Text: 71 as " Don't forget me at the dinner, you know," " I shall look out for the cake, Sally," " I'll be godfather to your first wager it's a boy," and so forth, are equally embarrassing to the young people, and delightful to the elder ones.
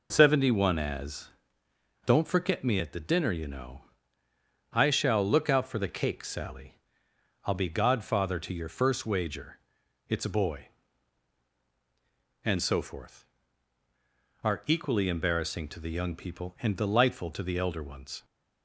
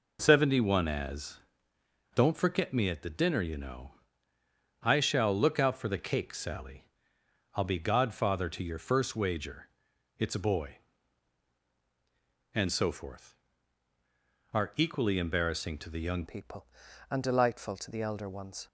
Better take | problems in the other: first | pauses between "wager" and "it's"; noticeable; at 9.7 s; 0.48 s long; noticeable in the first // changes voice at "people"; from 16.2 s on; 2.4 s long

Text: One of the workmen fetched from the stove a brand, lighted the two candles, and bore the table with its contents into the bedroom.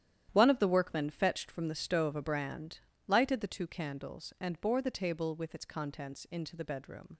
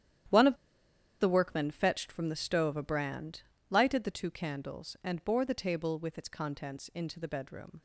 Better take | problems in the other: first | starts louder than the rest; strong; until 1.9 s; 11 dB; strong in the first // pauses between "of" and "the"; noticeable; at 0.5 s; 0.64 s long

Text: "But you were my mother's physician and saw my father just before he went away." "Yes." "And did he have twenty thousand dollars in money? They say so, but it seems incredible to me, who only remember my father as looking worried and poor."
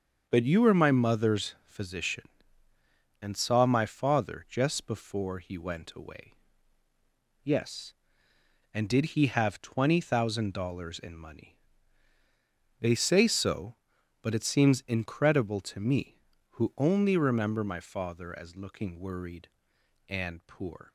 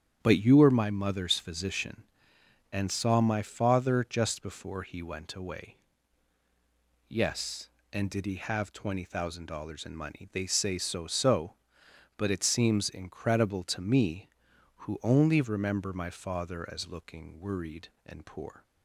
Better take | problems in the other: first | starts louder than the rest; strong; until 1.2 s; 9.5 dB; also in the first // says "so" twice; at 11.0 s

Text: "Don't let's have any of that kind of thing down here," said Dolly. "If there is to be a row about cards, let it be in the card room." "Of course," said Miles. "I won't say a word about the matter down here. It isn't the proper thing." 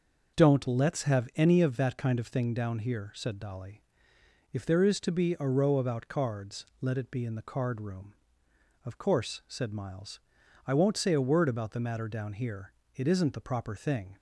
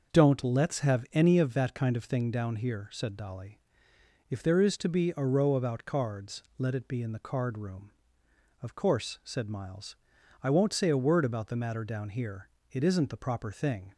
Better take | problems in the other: neither | none

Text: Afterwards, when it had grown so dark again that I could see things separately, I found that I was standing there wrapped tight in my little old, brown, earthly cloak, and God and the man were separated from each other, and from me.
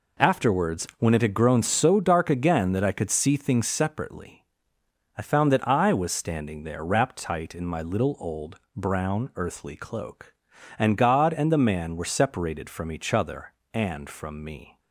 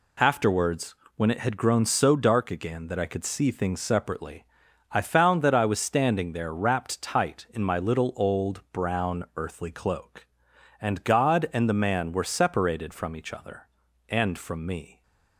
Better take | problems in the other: neither | none

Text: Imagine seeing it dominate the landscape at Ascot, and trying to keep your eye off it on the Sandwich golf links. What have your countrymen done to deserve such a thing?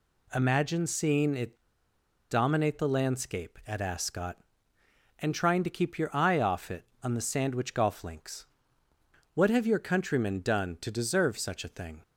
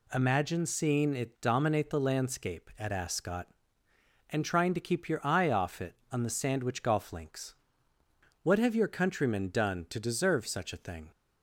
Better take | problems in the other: second | pauses between "it" and "dominate"; noticeable; at 1.6 s; 0.68 s long

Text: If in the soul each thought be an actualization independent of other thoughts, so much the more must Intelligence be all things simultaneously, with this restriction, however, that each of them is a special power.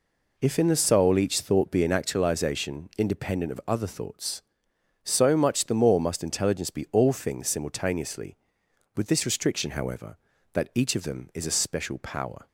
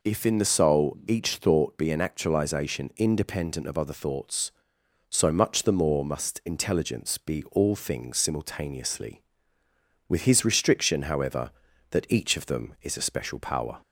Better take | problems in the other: first | says "his" for "this"; at 10.2 s

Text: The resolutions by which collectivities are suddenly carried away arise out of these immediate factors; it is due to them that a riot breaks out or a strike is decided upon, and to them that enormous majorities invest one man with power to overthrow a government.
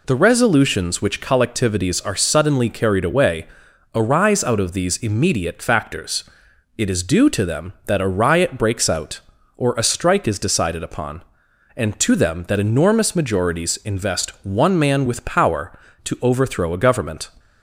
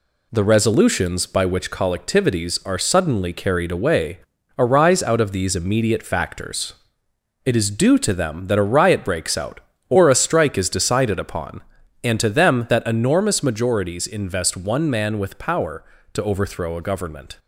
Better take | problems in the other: second | skips "by"; at 1.0 s // pauses between "away" and "arise"; noticeable; at 3.4 s; 0.48 s long; also in the second

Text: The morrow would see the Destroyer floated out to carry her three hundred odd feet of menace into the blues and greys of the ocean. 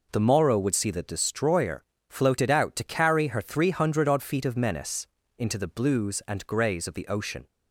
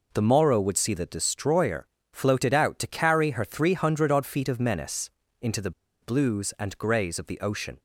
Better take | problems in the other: first | pauses between "Destroyer" and "floated"; slight; at 1.8 s; 0.26 s long; slight in the first // pauses between "menace" and "into"; slight; at 5.0 s; 0.32 s long; slight in the first // pauses between "the" and "blues"; slight; at 5.7 s; 0.31 s long

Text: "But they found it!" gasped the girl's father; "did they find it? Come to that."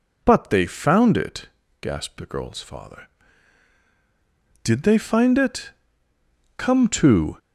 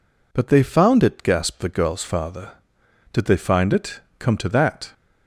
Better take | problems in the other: second | stops before "that"; at 7.3 s

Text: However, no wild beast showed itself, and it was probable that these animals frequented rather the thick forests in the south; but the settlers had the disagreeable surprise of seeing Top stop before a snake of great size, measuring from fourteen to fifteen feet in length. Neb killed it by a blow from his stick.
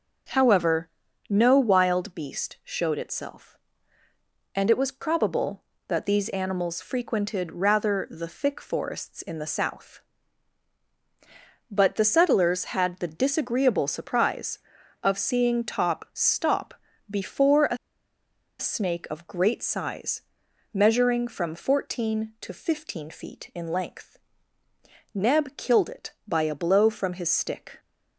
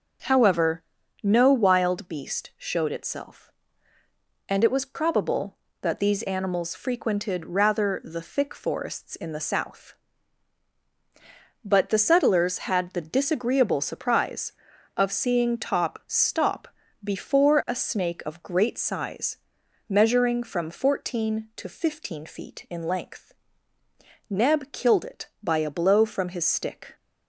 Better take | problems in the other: second | pauses between "stop" and "before"; slight; at 16.7 s; 0.36 s long; slight in the second // pauses between "a" and "snake"; noticeable; at 17.7 s; 0.82 s long

